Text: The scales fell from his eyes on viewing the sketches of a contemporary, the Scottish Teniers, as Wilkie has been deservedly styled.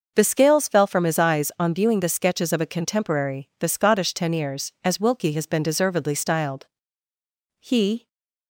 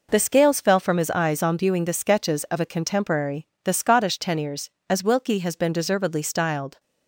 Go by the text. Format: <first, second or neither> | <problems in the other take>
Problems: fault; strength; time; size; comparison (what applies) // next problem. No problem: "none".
second | goes on to say "He"; slight; from 7.5 s on; 0.48 s long // stays silent after the last word; slight; from 7.9 s on; 0.5 s long